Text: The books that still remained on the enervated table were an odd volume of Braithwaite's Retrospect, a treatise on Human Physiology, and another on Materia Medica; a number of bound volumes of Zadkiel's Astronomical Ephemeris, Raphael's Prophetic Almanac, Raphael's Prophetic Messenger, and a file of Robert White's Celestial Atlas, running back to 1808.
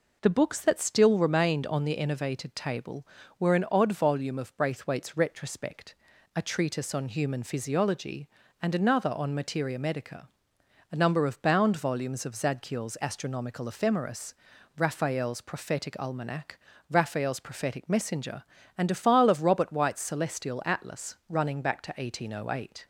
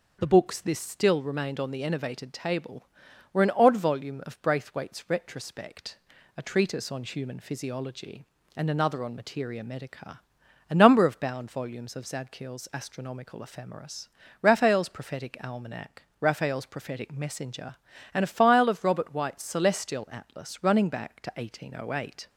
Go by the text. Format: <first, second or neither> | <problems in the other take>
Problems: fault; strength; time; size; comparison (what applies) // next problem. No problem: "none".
first | says "this" for "that"; at 0.6 s